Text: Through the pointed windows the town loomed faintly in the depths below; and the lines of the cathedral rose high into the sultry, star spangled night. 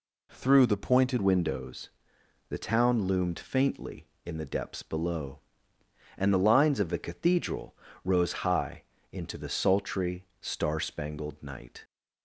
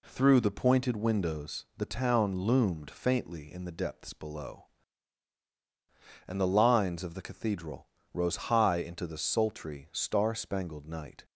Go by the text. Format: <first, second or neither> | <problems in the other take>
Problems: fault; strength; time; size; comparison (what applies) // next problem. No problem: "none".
second | changes voice at "windows"; from 1.1 s on; 10.7 s long // pauses between "windows" and "the"; noticeable; at 1.8 s; 0.58 s long // pauses between "cathedral" and "rose"; slight; at 7.7 s; 0.26 s long; slight in the second // pauses between "high" and "into"; slight; at 8.8 s; 0.28 s long